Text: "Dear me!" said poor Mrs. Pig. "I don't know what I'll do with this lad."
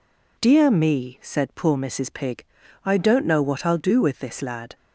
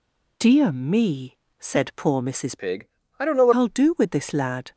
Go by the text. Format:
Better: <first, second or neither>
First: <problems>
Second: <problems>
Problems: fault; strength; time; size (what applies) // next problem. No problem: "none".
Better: first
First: none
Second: changes voice from "Pig" to "what"; from 2.5 to 3.5 s; 1.0 s long